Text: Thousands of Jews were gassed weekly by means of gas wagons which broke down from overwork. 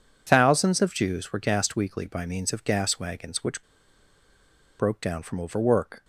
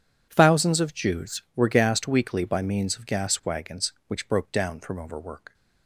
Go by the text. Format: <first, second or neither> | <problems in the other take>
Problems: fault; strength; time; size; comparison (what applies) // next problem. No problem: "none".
second | pauses between "which" and "broke"; at 3.6 s; 1.1 s long